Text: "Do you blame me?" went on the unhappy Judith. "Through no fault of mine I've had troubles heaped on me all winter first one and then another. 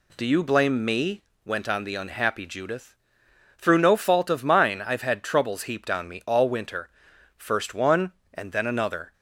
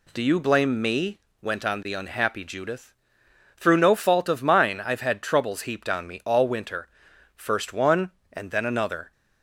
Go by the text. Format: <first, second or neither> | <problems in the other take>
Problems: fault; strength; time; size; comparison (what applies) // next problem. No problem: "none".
neither | pauses between "winter" and "first"; noticeable; the same in both